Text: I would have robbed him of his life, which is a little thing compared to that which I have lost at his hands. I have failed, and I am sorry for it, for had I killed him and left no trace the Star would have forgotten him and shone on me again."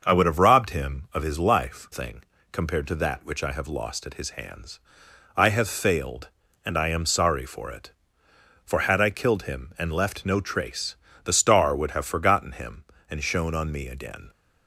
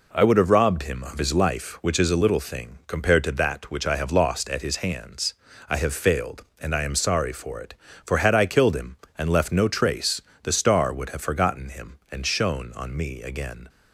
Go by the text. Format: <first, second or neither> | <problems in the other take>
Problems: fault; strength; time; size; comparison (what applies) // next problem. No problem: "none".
second | starts louder than the rest; until 1.0 s; 6.5 dB // skips "which is a little"; at 1.8 s // pauses between "thing" and "compared"; slight; at 2.2 s; 0.30 s long // pauses between "trace" and "the"; slight; at 10.9 s; 0.28 s long; slight in the second